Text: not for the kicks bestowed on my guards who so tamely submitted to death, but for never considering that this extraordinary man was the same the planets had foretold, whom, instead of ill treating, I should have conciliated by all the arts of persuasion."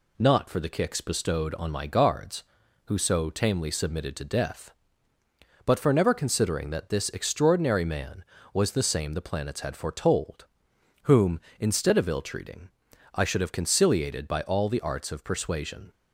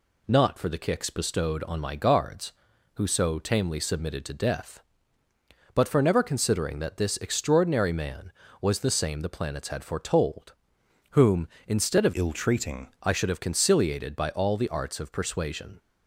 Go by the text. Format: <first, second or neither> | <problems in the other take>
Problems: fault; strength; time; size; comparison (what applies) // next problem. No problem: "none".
first | changes voice from "ill" to "treating"; from 12.1 to 12.8 s; 0.7 s long